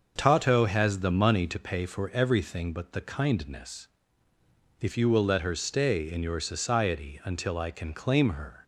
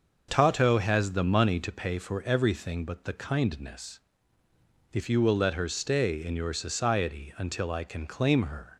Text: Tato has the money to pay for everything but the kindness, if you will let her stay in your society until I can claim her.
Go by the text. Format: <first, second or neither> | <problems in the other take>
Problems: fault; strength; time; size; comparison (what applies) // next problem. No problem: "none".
neither | starts louder than the rest; the same in both